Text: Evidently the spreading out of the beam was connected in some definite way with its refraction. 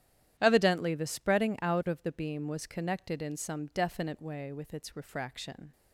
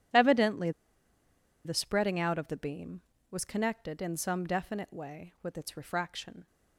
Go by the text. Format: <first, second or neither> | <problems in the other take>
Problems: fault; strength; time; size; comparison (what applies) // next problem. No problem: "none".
first | starts louder than the rest; strong; until 2.0 s; 11 dB; strong in the first // pauses between "Evidently" and "the"; noticeable; at 0.7 s; 0.94 s long